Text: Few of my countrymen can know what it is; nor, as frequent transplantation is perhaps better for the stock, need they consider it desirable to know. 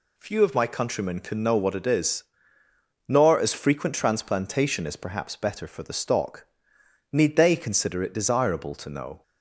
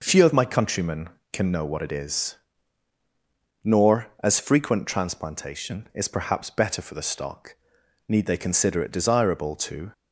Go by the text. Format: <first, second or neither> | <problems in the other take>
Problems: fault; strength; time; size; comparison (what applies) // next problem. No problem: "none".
first | stops before "know"; at 9.9 s